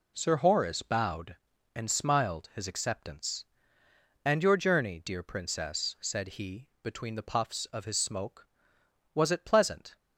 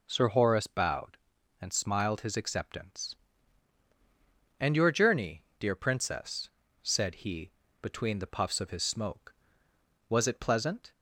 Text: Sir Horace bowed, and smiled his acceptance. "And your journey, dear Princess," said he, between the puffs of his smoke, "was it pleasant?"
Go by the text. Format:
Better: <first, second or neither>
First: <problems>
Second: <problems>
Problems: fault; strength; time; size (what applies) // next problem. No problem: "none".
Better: neither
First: none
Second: none